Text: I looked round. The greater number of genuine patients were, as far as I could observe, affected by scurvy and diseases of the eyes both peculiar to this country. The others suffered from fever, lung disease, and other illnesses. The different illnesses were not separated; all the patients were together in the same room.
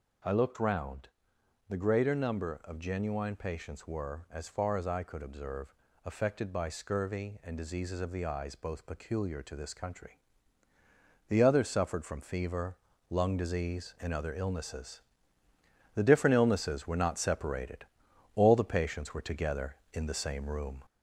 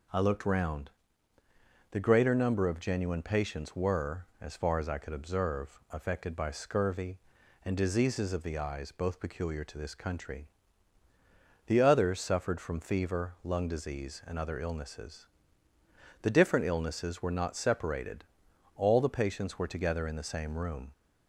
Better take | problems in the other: second | gets louder; slight; throughout; 3 dB

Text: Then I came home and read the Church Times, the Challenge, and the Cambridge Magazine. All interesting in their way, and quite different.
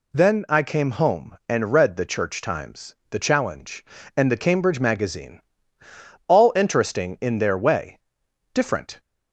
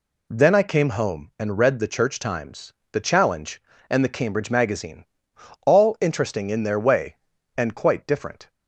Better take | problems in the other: second | skips "and quite"; at 8.2 s

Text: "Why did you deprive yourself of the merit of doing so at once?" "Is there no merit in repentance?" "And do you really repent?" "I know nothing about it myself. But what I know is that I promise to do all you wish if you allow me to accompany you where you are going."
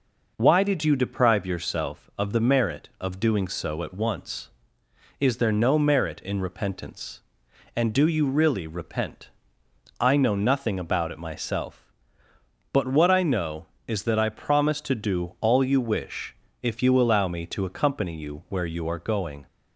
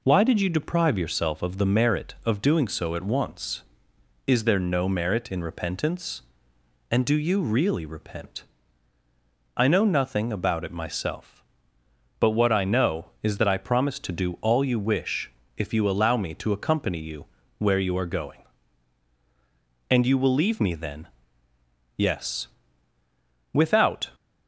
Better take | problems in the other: first | pauses between "wish" and "if"; slight; at 15.2 s; 0.26 s long; slight in the first // pauses between "you" and "where"; slight; at 17.2 s; 0.34 s long // goes on to say "And you will leave me then Yes Without"; strong; from 19.8 s on; 4.2 s long

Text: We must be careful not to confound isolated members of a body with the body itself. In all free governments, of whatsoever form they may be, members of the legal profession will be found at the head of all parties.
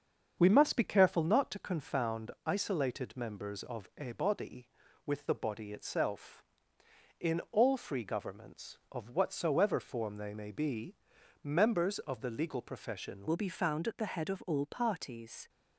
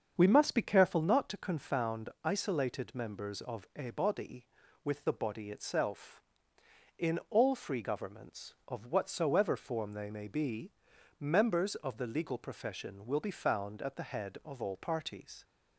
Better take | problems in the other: second | starts louder than the rest; until 1.3 s; 7 dB; also in the second // pauses between "confound" and "isolated"; slight; at 2.3 s; 0.16 s long; slight in the second // changes voice at "will"; from 13.2 s on; 2.2 s long

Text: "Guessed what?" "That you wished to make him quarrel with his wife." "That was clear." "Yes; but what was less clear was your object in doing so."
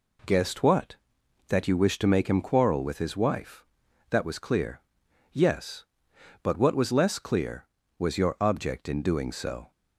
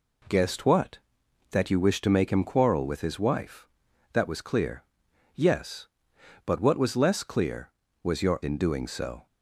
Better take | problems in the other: first | skips "object"; at 8.4 s

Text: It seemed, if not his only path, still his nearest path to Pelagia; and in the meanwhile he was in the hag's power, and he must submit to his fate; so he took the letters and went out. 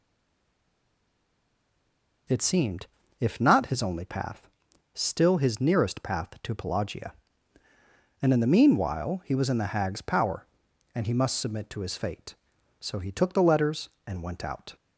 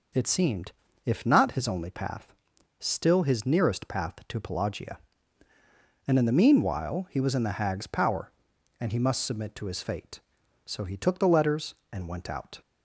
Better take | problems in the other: second | stays silent before the first word; until 2.2 s; 2.2 s long

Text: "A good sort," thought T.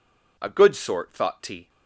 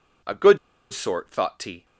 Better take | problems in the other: first | pauses between "good" and "sort"; slight; at 0.5 s; 0.34 s long

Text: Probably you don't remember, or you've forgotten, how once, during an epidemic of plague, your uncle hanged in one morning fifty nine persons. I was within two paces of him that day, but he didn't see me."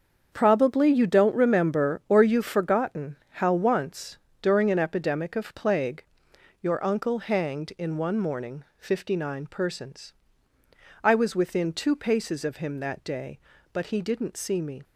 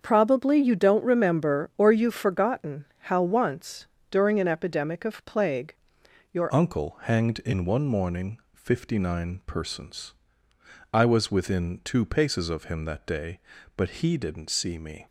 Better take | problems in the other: first | starts louder than the rest; until 1.0 s; 6.5 dB; also in the first // changes voice at "uncle"; from 6.4 s on; 8.6 s long // pauses between "morning" and "fifty"; slight; at 8.3 s; 0.16 s long

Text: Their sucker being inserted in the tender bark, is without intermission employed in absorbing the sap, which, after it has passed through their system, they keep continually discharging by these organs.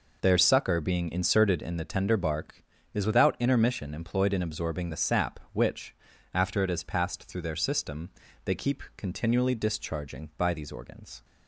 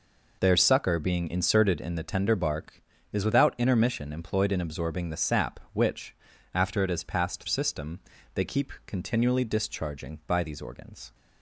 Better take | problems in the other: first | skips "through their"; at 7.4 s

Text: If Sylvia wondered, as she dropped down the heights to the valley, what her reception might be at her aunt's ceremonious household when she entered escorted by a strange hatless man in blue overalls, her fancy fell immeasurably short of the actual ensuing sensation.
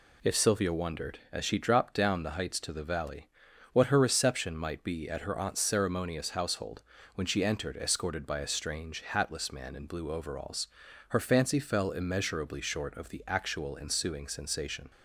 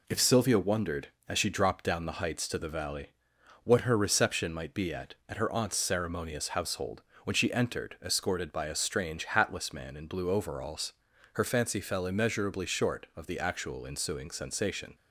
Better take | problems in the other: first | says "at" twice; at 5.2 s // pauses between "household" and "when"; slight; at 7.0 s; 0.22 s long; slight in the first

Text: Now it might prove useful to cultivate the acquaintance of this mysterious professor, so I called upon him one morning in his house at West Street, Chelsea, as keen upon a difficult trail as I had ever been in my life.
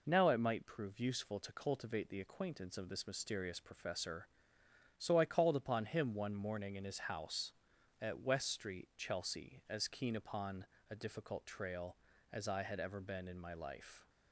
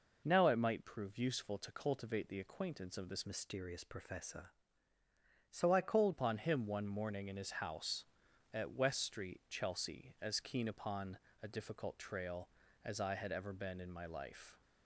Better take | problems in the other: first | changes voice from "mysterious" to "called"; from 3.2 to 6.1 s; 2.9 s long // pauses between "upon" and "a"; slight; at 11.1 s; 0.24 s long; slight in the first

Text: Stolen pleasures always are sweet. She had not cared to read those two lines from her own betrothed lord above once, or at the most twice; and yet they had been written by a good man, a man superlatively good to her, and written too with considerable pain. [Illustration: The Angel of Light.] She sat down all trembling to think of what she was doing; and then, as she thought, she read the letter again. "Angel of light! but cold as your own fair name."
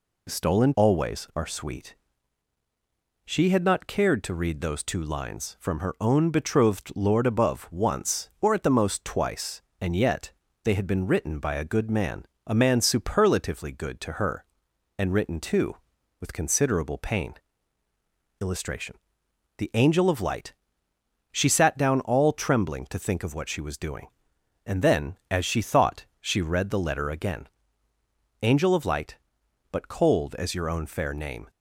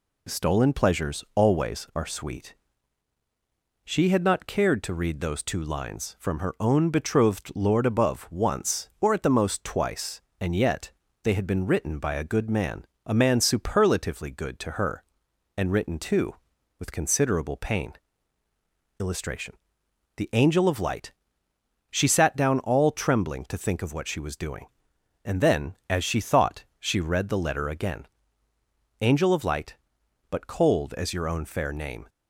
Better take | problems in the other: second | skips "pleasures"; at 0.7 s // pauses between "yet" and "they"; slight; at 10.3 s; 0.32 s long; slight in the second

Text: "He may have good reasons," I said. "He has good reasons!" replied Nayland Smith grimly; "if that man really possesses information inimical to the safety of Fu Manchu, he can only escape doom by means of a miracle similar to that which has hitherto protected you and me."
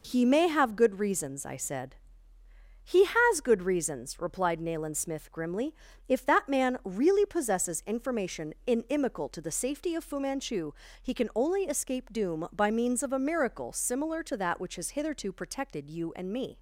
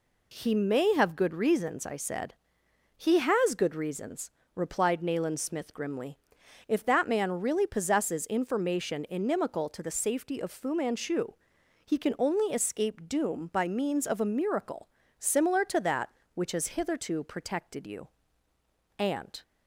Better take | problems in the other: first | pauses between "miracle" and "similar"; slight; at 14.8 s; 0.30 s long // stops before "me"; at 19.4 s

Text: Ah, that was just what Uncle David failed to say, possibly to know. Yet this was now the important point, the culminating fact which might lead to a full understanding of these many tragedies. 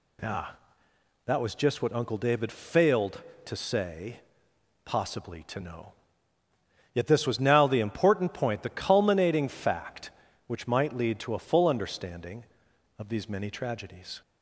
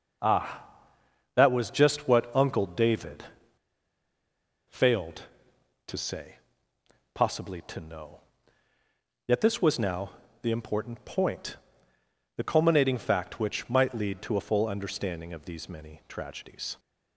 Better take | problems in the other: first | pauses between "David" and "failed"; strong; at 3.2 s; 1.4 s long // pauses between "now" and "the"; slight; at 10.1 s; 0.30 s long

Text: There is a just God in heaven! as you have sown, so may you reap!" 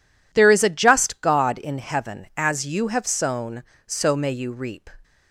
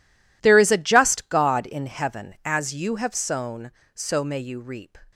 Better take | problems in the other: first | gets quieter; strong; throughout; 16.5 dB

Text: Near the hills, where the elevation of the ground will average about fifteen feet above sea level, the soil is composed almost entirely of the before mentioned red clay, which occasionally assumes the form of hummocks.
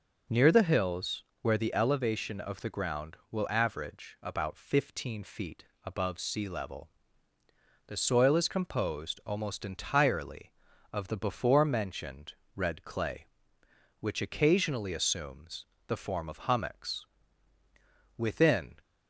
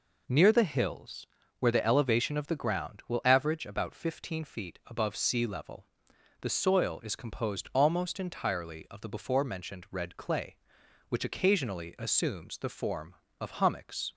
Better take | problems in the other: second | pauses between "feet" and "above"; slight; at 5.6 s; 0.22 s long // pauses between "mentioned" and "red"; slight; at 12.3 s; 0.24 s long // pauses between "assumes" and "the"; slight; at 15.6 s; 0.24 s long // goes on to say "Within"; from 18.1 s on; 0.58 s long

